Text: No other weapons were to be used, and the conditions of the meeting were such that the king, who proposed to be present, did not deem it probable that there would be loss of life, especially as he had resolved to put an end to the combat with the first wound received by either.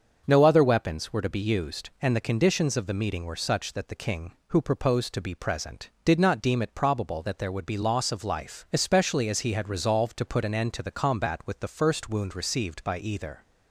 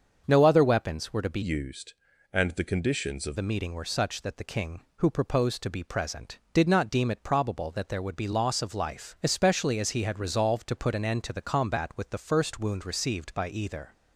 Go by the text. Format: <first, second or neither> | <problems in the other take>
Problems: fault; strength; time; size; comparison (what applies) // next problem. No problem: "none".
first | starts louder than the rest; until 1.2 s; 7 dB; also in the first // changes voice from "used" to "of"; from 1.4 to 3.3 s; 1.9 s long